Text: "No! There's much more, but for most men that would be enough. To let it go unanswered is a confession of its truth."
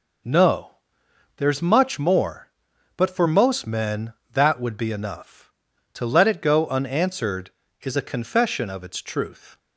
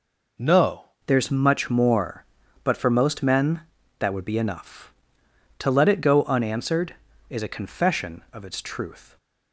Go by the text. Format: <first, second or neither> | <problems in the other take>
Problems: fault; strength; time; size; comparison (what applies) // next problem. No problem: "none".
first | changes voice at "There's"; from 1.0 s on; 8.1 s long